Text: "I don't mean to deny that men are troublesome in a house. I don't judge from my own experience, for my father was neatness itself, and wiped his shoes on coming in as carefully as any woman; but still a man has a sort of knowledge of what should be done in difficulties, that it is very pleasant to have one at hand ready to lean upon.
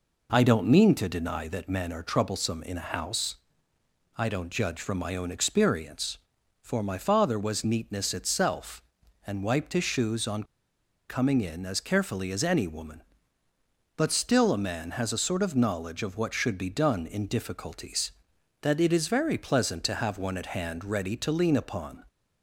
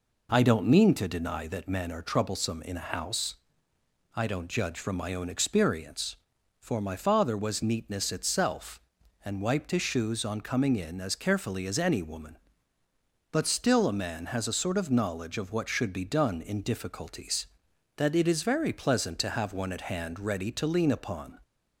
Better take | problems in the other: second | pauses between "on" and "coming"; noticeable; at 10.4 s; 0.63 s long

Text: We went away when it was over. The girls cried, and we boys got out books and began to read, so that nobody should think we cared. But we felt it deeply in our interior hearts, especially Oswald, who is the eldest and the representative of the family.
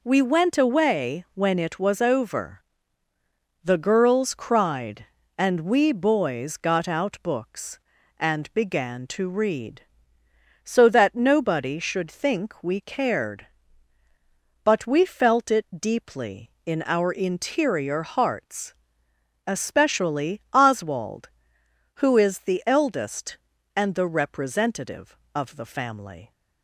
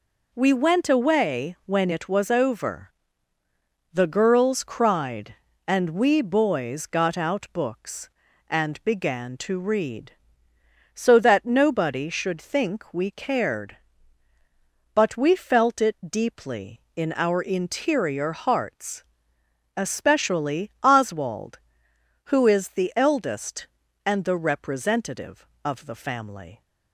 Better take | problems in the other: neither | none

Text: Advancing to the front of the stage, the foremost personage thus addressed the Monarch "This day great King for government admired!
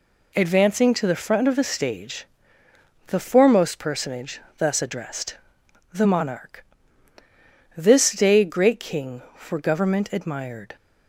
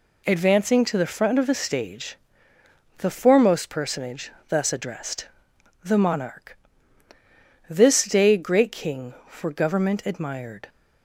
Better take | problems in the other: neither | pauses between "personage" and "thus"; slight; the same in both // pauses between "addressed" and "the"; noticeable; the same in both // pauses between "Monarch" and "This"; the same in both

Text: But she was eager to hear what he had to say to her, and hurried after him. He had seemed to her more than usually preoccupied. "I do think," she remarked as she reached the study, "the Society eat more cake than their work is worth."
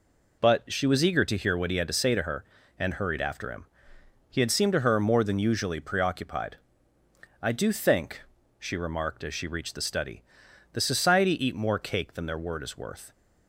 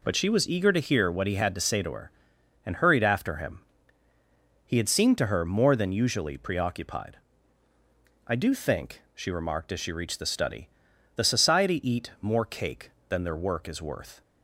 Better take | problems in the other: second | says "word" for "work"; at 12.3 s

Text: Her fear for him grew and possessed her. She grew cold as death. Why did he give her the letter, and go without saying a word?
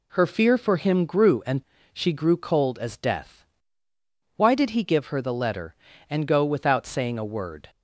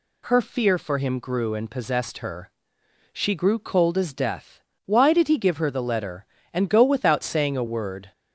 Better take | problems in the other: second | skips "possessed her"; at 1.7 s

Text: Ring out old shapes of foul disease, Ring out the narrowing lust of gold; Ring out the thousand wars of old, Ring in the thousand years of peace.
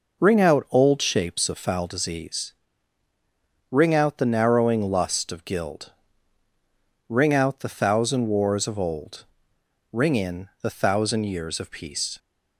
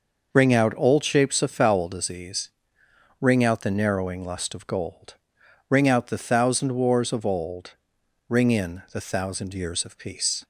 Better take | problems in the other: second | says "guild" for "gold"; at 5.4 s

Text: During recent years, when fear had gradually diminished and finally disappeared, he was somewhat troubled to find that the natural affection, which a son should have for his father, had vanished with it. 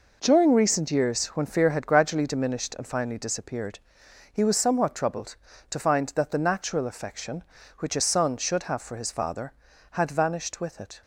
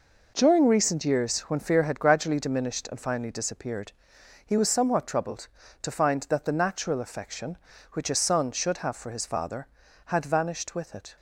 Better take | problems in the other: neither | none

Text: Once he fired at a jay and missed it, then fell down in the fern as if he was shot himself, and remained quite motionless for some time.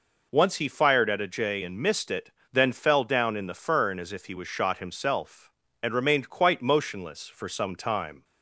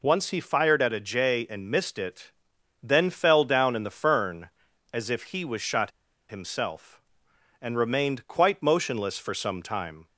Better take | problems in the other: first | pauses between "shot" and "himself"; at 5.9 s; 0.38 s long

